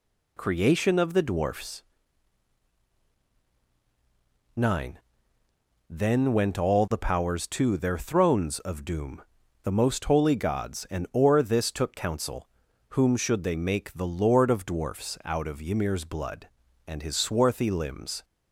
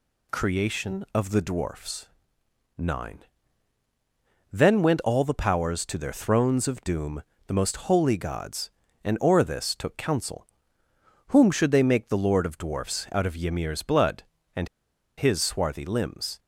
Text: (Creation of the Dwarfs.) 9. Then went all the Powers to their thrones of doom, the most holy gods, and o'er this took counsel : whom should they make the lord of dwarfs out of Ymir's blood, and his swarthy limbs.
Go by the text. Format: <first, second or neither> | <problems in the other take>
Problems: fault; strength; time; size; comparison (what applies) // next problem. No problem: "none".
first | pauses between "and" and "his"; noticeable; at 14.6 s; 0.50 s long